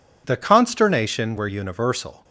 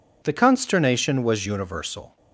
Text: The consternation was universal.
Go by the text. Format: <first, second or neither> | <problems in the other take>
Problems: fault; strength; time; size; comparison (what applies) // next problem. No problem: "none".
second | says "were" for "was"; at 1.3 s